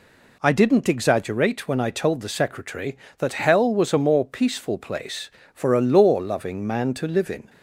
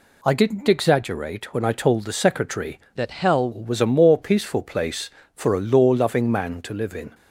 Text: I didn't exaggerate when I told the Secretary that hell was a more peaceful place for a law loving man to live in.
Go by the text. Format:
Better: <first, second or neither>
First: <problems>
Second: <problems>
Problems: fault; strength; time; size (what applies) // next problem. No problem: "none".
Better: first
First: none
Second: changes voice from "that" to "hell"; from 2.9 to 3.5 s; 0.6 s long